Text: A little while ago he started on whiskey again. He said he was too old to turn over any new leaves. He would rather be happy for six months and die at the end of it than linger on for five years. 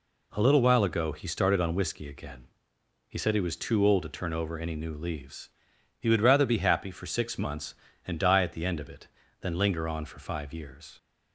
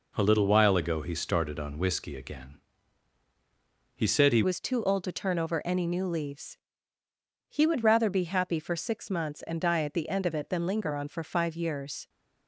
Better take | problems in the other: first | changes voice at "was"; from 4.4 s on; 7.6 s long

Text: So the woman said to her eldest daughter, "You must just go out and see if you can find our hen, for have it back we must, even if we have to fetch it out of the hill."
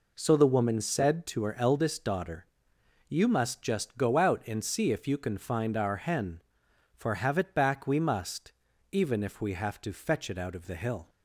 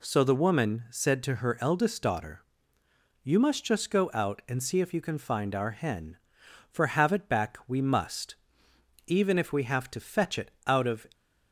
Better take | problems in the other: first | stops before "the hill"; at 11.1 s

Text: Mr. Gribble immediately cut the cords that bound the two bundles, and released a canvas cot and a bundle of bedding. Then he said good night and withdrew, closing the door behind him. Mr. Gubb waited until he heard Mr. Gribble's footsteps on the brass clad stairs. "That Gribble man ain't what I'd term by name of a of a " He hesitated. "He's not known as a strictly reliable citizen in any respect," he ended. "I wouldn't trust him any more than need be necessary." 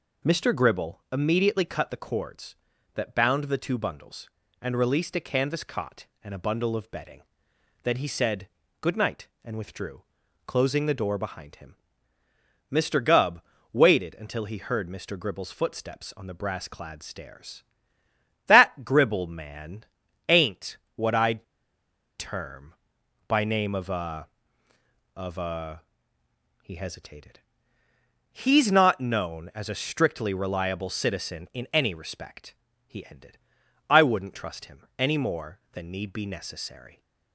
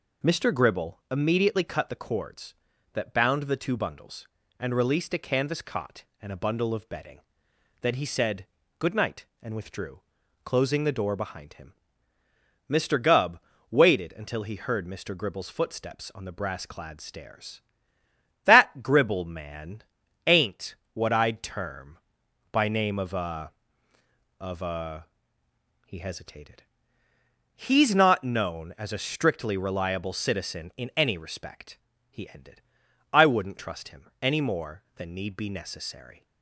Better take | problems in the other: second | pauses between "said" and "good"; slight; at 8.4 s; 0.32 s long; slight in the second // pauses between "Gubb" and "waited"; slight; at 13.4 s; 0.32 s long; slight in the second // pauses between "man" and "ain't"; noticeable; at 19.8 s; 0.46 s long; noticeable in the second // pauses between "ain't" and "what"; slight; at 20.7 s; 0.18 s long; slight in the second // pauses between "I'd" and "term"; noticeable; at 21.4 s; 0.75 s long

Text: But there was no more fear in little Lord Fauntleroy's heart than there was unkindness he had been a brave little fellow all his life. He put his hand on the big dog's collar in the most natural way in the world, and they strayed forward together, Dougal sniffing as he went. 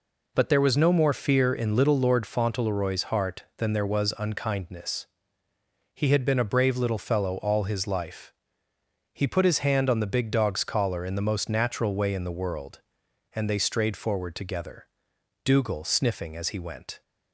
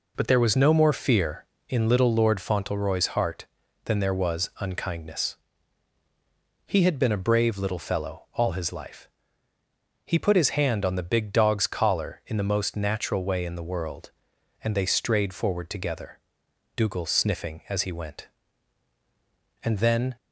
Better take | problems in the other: first | pauses between "unkindness" and "he"; strong; at 5.3 s; 1.3 s long; noticeable in the first // goes on to say "And then"; from 19.6 s on; 0.52 s long

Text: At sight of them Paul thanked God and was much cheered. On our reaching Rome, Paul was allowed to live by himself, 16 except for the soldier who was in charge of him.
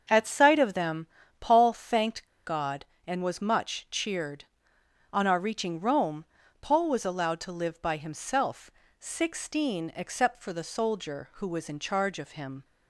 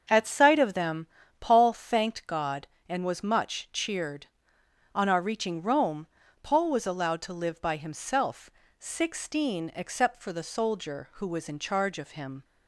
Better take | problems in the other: second | starts louder than the rest; until 1.4 s; 6.5 dB; also in the second // pauses between "them" and "Paul"; slight; at 1.0 s; 0.32 s long; slight in the second // pauses between "thanked" and "God"; slight; at 2.2 s; 0.20 s long

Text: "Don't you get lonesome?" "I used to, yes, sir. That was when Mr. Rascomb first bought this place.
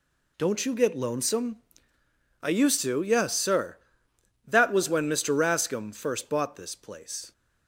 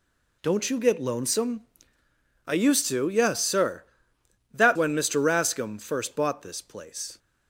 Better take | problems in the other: first | skips "was"; at 4.7 s

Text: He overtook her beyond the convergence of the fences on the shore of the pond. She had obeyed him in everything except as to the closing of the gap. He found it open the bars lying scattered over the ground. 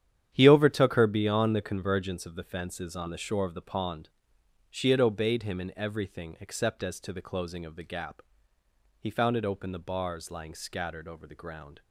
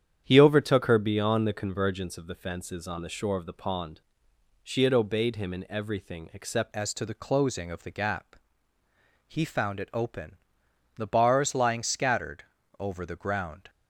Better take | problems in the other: first | starts louder than the rest; strong; until 1.2 s; 9 dB; strong in the first // changes voice at "as"; from 6.7 s on; 6.9 s long // pauses between "open" and "the"; noticeable; at 10.3 s; 0.60 s long // pauses between "scattered" and "over"; slight; at 12.4 s; 0.34 s long

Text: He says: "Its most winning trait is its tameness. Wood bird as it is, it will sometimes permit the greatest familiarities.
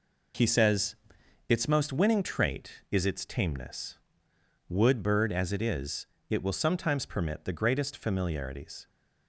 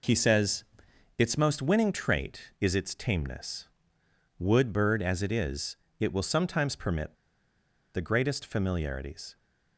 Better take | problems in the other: first | pauses between "permit" and "the"; noticeable; at 7.1 s; 0.80 s long

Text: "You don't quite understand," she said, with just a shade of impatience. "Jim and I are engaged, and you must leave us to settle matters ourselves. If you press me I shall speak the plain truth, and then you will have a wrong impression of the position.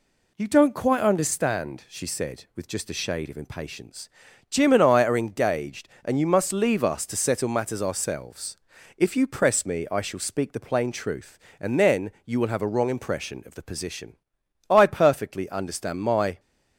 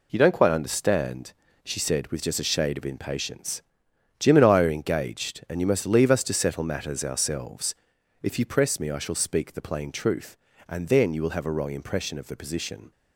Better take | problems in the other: second | pauses between "then" and "you"; slight; at 12.0 s; 0.16 s long // goes on to say "I perfectly understand my"; strong; from 14.7 s on; 1.6 s long

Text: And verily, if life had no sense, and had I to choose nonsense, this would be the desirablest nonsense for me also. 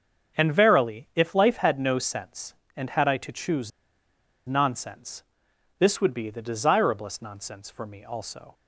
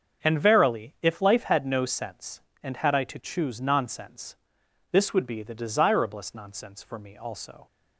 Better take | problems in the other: second | starts louder than the rest; until 1.4 s; 7 dB; also in the second // pauses between "choose" and "nonsense"; noticeable; at 3.7 s; 0.77 s long

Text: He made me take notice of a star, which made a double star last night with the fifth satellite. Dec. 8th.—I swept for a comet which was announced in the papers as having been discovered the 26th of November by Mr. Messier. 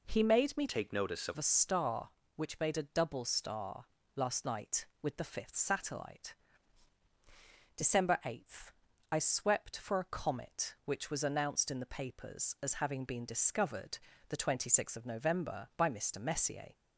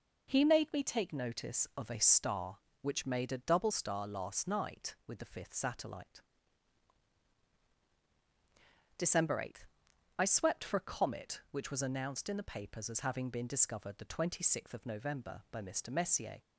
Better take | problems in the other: second | changes voice from "take" to "of"; from 0.6 to 1.3 s; 0.7 s long // pauses between "star" and "last"; slight; at 3.8 s; 0.30 s long // pauses between "discovered" and "the"; slight; at 13.9 s; 0.32 s long

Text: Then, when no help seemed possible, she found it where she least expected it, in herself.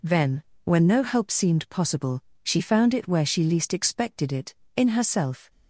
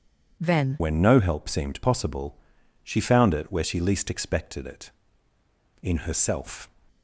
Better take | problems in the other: first | changes voice at "when"; from 0.7 s on; 5.9 s long

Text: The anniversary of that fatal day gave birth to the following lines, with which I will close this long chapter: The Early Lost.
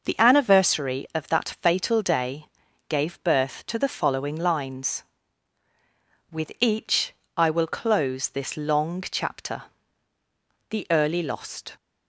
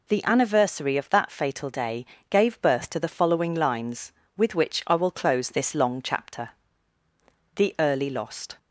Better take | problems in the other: second | pauses between "day" and "gave"; at 2.4 s; 0.42 s long; slight in the second // says "each" for "which"; at 6.5 s

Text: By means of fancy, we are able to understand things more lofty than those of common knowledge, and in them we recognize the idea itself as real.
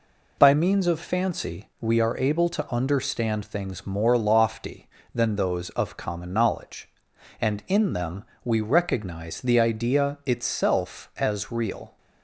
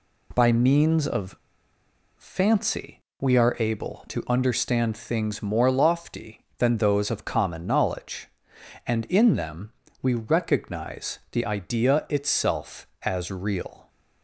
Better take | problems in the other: first | pauses between "of" and "fancy"; noticeable; at 1.3 s; 0.82 s long // pauses between "them" and "we"; slight; at 9.7 s; 0.30 s long; slight in the first

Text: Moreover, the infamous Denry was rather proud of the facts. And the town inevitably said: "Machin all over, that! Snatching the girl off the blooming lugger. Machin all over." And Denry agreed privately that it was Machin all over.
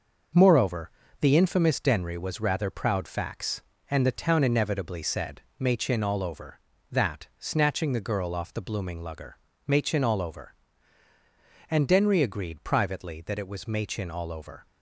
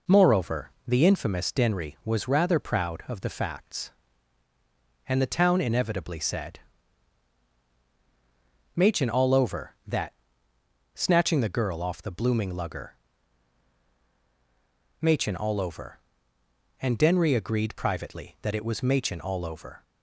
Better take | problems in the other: second | skips "of the"; at 3.0 s

